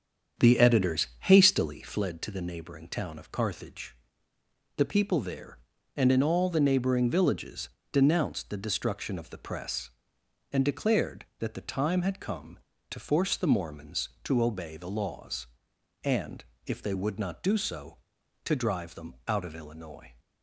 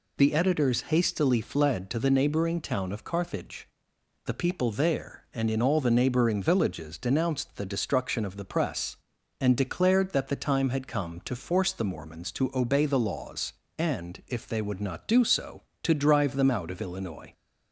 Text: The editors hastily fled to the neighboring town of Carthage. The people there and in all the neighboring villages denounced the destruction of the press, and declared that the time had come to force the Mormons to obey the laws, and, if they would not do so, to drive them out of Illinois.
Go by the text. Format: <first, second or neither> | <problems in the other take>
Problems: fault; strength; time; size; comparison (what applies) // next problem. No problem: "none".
second | starts louder than the rest; strong; until 2.0 s; 8 dB // pauses between "villages" and "denounced"; slight; at 7.6 s; 0.22 s long